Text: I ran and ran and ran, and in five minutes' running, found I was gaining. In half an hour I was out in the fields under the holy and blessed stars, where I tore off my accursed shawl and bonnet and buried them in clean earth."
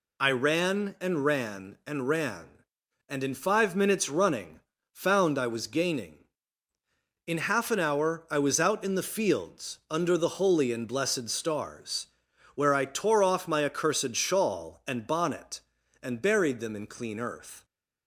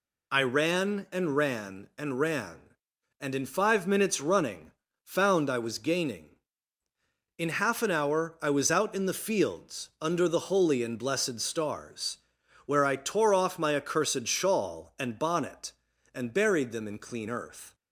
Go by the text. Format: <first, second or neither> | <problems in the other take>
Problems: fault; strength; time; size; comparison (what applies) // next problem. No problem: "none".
neither | none